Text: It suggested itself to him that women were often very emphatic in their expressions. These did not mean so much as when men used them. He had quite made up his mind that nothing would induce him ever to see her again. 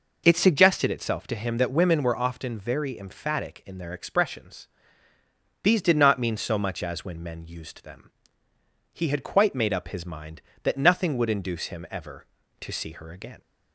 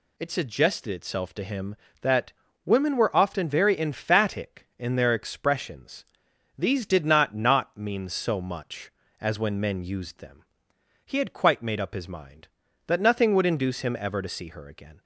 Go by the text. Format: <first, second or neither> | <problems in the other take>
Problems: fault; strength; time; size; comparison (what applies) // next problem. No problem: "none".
first | pauses between "that" and "women"; slight; at 2.3 s; 0.32 s long // says "not" twice; at 7.3 s